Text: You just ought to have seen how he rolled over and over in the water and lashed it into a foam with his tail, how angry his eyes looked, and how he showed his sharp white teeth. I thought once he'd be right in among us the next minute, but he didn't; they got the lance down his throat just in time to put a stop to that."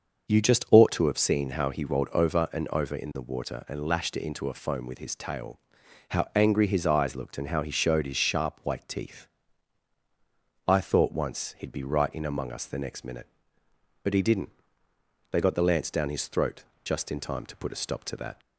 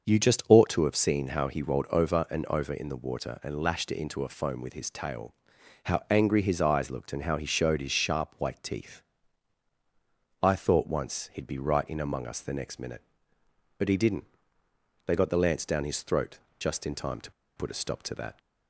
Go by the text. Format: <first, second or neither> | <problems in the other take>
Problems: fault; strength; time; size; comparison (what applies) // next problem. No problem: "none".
first | starts louder than the rest; until 1.1 s; 6.5 dB; also in the first // pauses between "throat" and "just"; slight; at 16.3 s; 0.22 s long; slight in the first // pauses between "to" and "put"; slight; at 17.3 s; 0.25 s long